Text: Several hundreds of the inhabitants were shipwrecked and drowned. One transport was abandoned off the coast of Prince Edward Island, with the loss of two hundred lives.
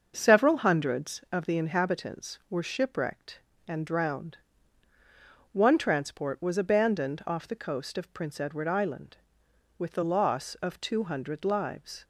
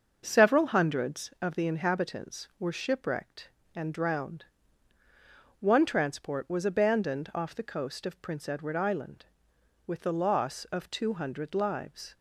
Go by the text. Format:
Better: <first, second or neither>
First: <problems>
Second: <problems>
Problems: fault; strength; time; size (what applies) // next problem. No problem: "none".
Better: neither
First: starts louder than the rest; until 1.1 s; 6.5 dB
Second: starts louder than the rest; until 1.2 s; 6.5 dB